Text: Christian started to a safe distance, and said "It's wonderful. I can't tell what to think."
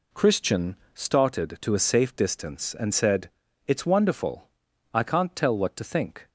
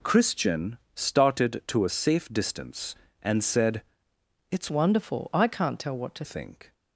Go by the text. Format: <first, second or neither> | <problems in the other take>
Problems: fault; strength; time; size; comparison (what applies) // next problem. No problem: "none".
first | pauses between "Christian" and "started"; slight; at 0.7 s; 0.18 s long; slight in the first // pauses between "said" and "It's"; noticeable; at 3.8 s; 0.66 s long; also in the first // changes voice from "wonderful" to "to"; from 4.6 to 6.2 s; 1.6 s long